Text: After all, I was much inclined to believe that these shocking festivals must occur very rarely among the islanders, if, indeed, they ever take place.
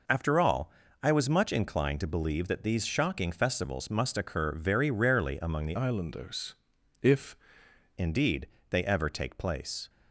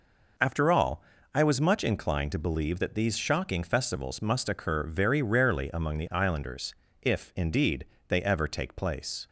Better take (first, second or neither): second